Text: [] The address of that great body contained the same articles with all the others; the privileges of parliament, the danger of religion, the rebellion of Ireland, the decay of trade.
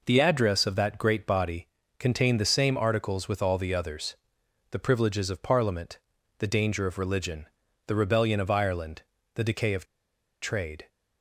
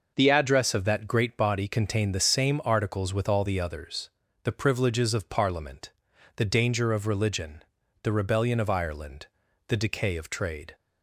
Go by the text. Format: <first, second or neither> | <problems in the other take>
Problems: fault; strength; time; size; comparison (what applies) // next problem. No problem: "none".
second | pauses between "body" and "contained"; slight; at 1.6 s; 0.30 s long // pauses between "of" and "trade"; noticeable; at 9.8 s; 0.57 s long